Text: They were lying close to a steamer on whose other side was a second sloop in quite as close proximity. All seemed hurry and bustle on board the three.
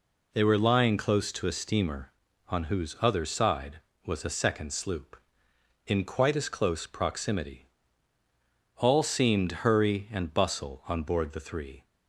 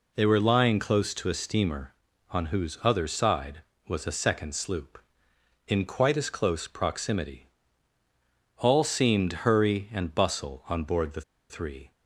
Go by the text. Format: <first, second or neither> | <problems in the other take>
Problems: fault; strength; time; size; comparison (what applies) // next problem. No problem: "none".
first | pauses between "the" and "three"; slight; at 11.2 s; 0.28 s long